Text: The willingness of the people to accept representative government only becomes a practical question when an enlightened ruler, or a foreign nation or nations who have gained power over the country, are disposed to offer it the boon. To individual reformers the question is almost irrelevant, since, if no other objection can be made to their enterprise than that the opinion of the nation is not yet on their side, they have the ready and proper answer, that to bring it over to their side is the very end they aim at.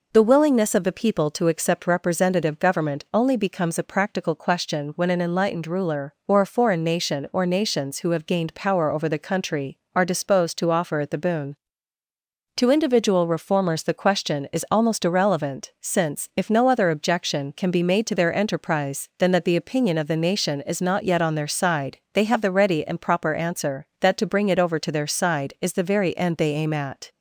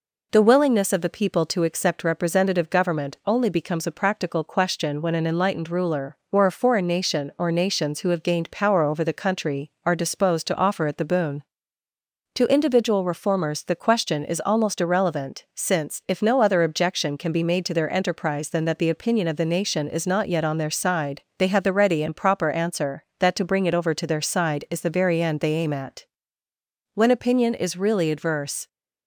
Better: first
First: none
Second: goes on to say "When opinion is really adverse"; strong; from 26.9 s on; 1.7 s long

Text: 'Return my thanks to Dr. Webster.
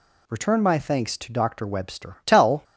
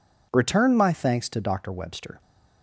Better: second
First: goes on to say "Tell"; slight; from 2.2 s on; 0.38 s long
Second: none

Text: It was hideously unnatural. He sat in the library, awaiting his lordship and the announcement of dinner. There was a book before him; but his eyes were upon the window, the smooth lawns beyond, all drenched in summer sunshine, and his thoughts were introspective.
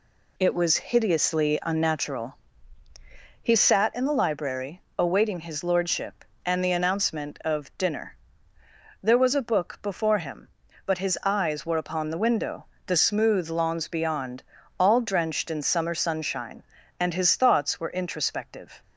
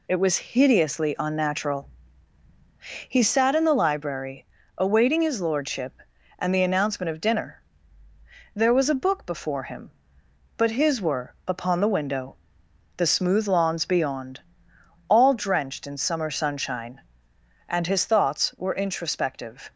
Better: first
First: none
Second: skips "eyes"; at 11.0 s

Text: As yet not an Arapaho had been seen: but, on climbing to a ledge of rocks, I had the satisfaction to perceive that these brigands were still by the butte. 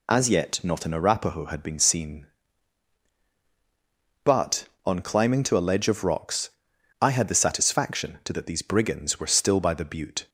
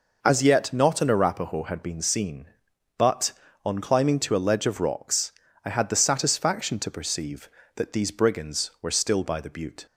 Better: second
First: skips "perceive"; at 8.3 s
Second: none

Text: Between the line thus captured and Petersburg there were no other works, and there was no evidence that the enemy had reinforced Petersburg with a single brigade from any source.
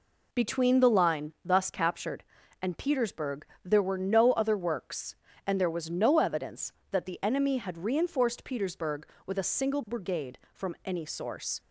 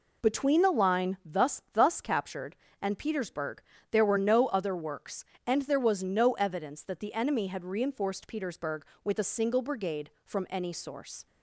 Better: first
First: pauses between "Petersburg" and "there"; slight; at 3.4 s; 0.20 s long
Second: says "thus" twice; at 1.7 s // pauses between "Petersburg" and "there"; slight; at 3.6 s; 0.30 s long

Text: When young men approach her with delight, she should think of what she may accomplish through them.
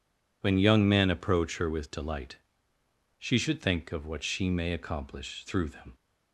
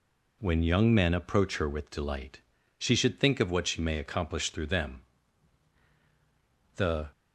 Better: first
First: none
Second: goes on to say "The"; slight; from 6.7 s on; 0.32 s long

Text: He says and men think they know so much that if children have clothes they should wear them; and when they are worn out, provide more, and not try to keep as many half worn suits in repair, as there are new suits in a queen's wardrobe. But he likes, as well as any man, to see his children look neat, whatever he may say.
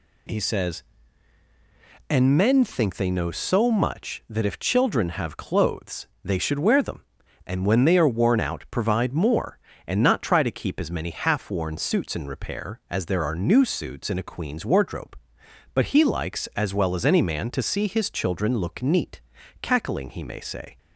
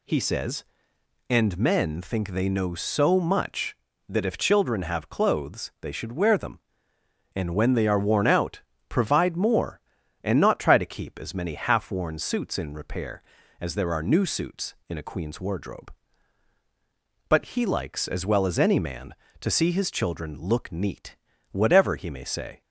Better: second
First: pauses between "clothes" and "they"; slight; at 6.0 s; 0.18 s long // says "cackling" for "whatever"; at 19.6 s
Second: none

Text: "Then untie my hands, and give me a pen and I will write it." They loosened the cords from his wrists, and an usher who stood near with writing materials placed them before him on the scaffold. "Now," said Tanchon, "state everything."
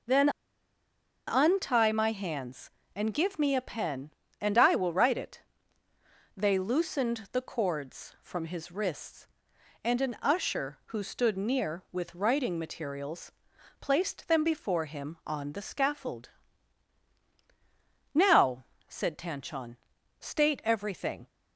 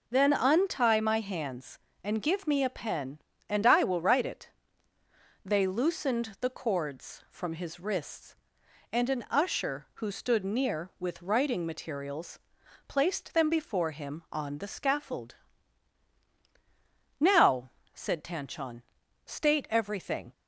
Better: second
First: pauses between "Then" and "untie"; at 0.2 s; 0.98 s long // pauses between "materials" and "placed"; noticeable; at 13.3 s; 0.50 s long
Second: pauses between "materials" and "placed"; noticeable; at 12.3 s; 0.50 s long

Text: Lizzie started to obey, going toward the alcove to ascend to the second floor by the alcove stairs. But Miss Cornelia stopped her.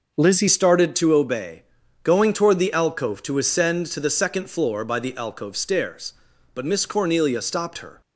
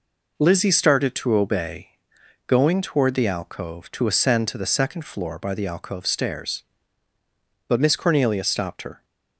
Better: second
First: changes voice at "started"; from 0.4 s on; 7.6 s long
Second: none

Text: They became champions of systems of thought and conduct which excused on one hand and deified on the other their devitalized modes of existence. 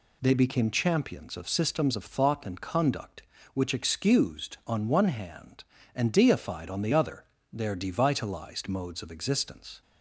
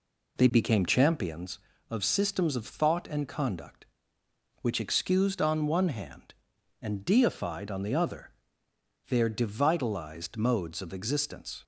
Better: first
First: pauses between "other" and "their"; slight; at 7.2 s; 0.26 s long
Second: starts louder than the rest; slight; until 1.4 s; 3 dB // pauses between "other" and "their"; noticeable; at 8.3 s; 0.76 s long

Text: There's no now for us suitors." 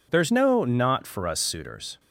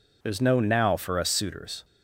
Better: second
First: says "not" for "now"; at 0.6 s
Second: none

